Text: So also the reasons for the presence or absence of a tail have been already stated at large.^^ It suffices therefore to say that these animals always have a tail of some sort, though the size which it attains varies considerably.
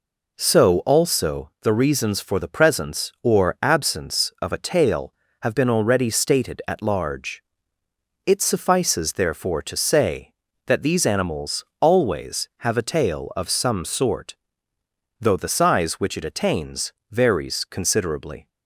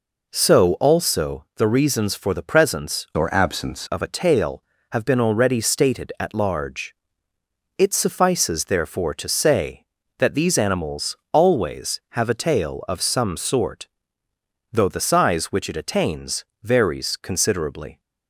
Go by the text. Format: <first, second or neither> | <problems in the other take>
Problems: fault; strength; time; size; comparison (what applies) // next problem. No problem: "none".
first | changes voice from "or" to "absence"; from 3.1 to 3.8 s; 0.7 s long // pauses between "animals" and "always"; slight; at 11.1 s; 0.16 s long; slight in the first // pauses between "attains" and "varies"; slight; at 16.4 s; 0.16 s long; slight in the first